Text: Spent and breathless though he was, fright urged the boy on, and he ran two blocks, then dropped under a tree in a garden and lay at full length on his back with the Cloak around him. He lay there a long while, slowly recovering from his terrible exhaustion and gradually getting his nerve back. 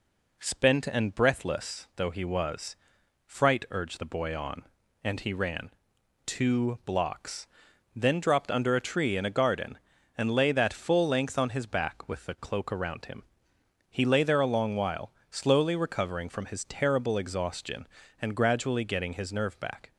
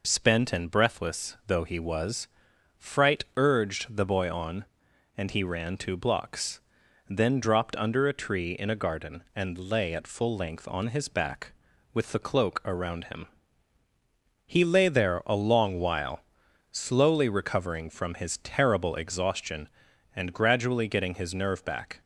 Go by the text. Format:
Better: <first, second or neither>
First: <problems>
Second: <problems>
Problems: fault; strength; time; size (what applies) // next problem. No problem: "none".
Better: second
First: pauses between "ran" and "two"; noticeable; at 5.7 s; 0.54 s long // says "that" for "at"; at 10.5 s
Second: none